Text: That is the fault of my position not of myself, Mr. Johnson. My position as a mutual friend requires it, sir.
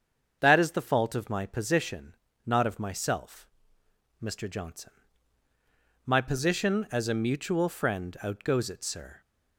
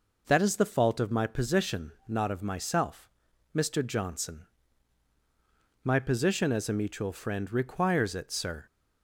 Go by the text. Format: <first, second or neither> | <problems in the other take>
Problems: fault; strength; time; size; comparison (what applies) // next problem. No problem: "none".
second | starts louder than the rest; until 1.4 s; 7 dB // pauses between "position" and "not"; slight; at 2.1 s; 0.32 s long; slight in the second // says "outgoes" for "requires"; at 8.2 s